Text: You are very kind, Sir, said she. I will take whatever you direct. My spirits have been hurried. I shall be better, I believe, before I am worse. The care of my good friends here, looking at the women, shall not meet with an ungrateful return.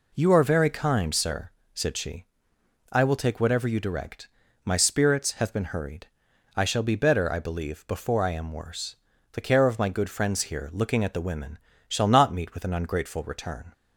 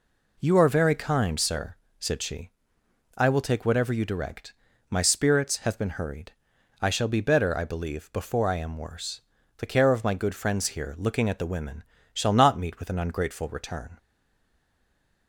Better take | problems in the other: first | stays silent after the last word; noticeable; from 13.9 s on; 1.3 s long

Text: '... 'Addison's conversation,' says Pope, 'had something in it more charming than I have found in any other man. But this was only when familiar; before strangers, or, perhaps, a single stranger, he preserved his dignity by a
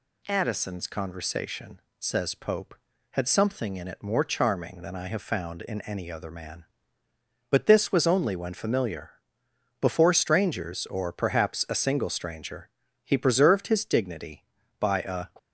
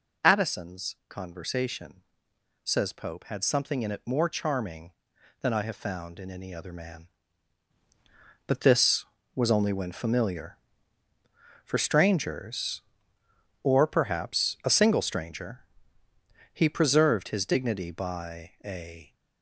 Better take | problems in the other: first | says "for" for "before"; at 11.6 s

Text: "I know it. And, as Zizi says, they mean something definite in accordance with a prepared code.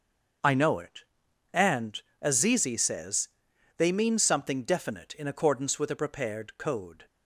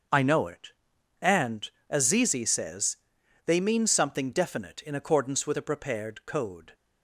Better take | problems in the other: neither | starts louder than the rest; the same in both

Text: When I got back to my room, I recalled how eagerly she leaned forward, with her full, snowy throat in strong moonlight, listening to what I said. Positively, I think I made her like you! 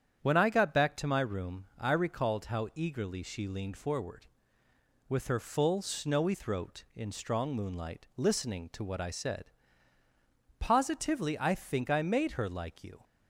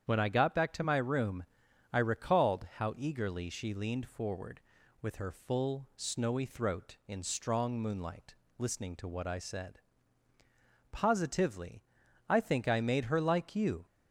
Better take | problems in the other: neither | starts louder than the rest; strong; the same in both

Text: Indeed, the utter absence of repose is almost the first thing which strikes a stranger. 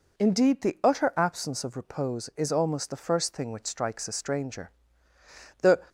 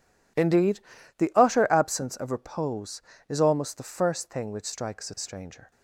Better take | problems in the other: second | goes on to say "The"; slight; from 5.5 s on; 0.22 s long

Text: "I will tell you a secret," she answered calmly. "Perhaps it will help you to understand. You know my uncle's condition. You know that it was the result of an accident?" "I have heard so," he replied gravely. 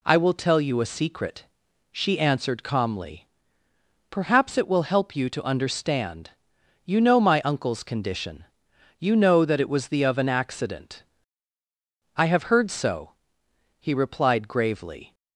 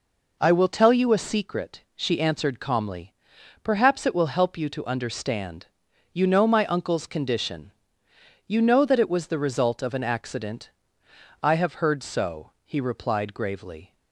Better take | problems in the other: second | skips "result"; at 10.0 s

